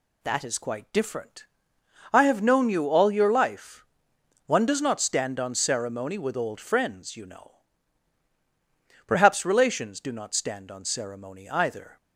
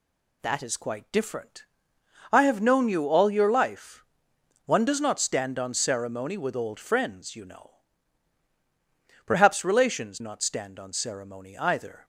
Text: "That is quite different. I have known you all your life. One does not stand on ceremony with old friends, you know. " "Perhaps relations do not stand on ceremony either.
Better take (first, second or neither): first